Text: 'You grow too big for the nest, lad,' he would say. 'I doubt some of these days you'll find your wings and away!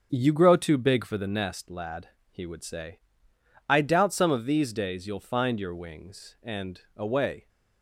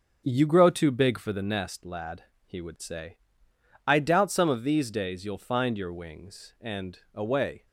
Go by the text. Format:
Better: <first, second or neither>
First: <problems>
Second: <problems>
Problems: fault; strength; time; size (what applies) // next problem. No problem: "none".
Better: neither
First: starts louder than the rest; until 1.1 s; 6.5 dB // pauses between "and" and "away"; slight; at 6.8 s; 0.16 s long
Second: starts louder than the rest; until 1.2 s; 6.5 dB // pauses between "and" and "away"; slight; at 6.9 s; 0.16 s long